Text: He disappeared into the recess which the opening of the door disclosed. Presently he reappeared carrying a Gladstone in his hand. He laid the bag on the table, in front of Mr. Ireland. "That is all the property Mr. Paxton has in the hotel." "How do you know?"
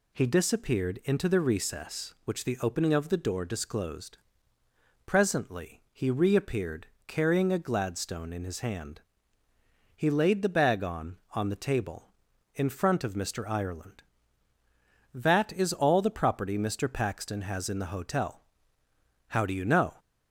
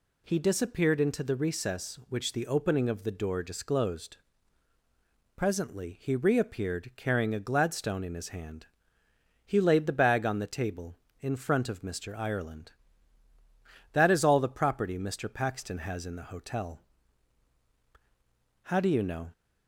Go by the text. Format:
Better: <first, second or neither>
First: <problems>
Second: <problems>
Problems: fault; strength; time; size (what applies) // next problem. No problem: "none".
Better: second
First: pauses between "reappeared" and "carrying"; slight; at 6.8 s; 0.20 s long // says "on" twice; at 11.3 s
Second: none